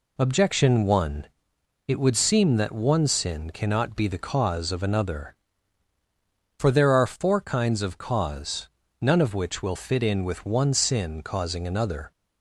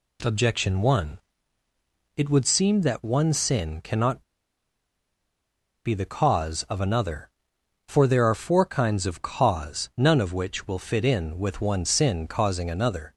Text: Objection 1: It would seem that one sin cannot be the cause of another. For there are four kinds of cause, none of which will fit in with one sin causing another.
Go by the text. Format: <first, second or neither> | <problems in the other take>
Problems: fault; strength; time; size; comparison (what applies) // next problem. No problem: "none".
first | pauses between "cannot" and "be"; strong; at 4.2 s; 1.6 s long